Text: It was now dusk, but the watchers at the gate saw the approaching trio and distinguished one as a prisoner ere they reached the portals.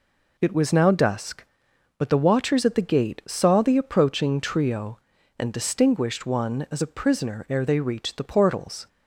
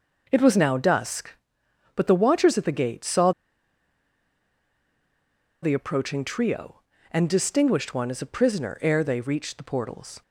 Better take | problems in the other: first | pauses between "saw" and "the"; strong; at 3.3 s; 2.3 s long

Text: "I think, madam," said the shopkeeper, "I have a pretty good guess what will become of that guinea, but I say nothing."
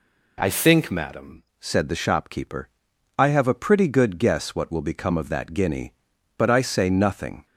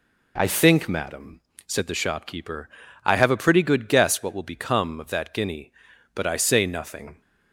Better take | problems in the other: second | changes voice at "said"; from 1.5 s on; 5.9 s long

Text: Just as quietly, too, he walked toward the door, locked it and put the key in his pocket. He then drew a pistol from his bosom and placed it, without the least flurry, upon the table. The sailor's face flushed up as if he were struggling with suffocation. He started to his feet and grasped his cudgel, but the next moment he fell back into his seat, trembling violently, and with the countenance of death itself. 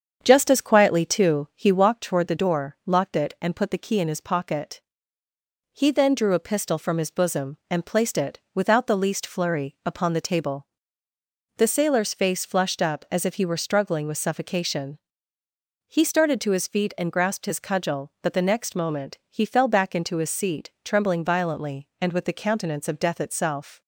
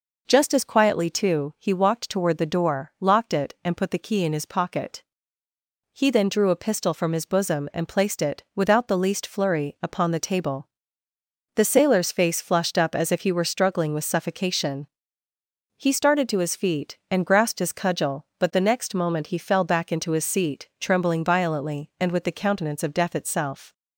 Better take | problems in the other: second | starts louder than the rest; strong; until 2.1 s; 7.5 dB

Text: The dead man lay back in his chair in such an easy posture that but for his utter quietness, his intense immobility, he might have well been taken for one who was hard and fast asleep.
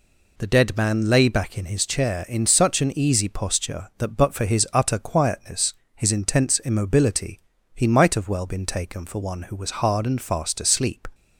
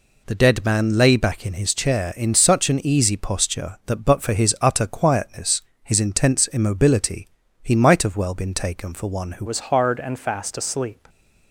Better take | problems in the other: first | changes voice at "was"; from 9.4 s on; 1.6 s long

